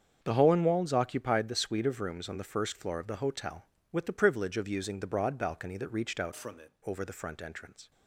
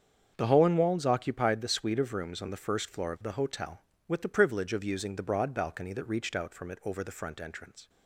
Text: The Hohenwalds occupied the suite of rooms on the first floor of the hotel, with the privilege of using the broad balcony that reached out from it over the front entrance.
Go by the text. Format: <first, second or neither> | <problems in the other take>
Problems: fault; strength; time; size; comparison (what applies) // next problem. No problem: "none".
second | starts louder than the rest; strong; until 1.2 s; 7.5 dB; strong in the second // changes voice from "from" to "it"; from 6.3 to 6.7 s; 0.4 s long